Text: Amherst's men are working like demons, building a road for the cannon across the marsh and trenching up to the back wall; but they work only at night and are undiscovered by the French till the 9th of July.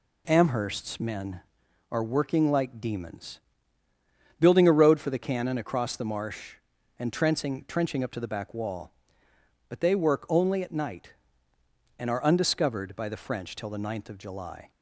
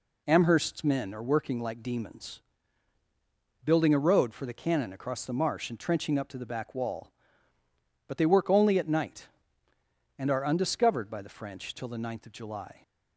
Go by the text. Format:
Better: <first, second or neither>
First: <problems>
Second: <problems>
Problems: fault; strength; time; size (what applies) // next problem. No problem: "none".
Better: second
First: says "trenching" twice; at 7.6 s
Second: none